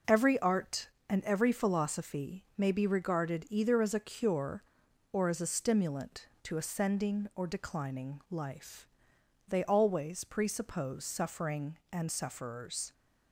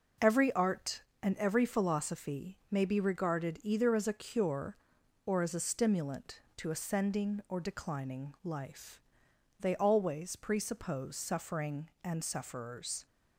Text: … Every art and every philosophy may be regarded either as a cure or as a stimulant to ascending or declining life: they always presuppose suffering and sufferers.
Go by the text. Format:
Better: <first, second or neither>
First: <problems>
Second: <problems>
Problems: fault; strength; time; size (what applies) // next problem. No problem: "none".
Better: neither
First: none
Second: none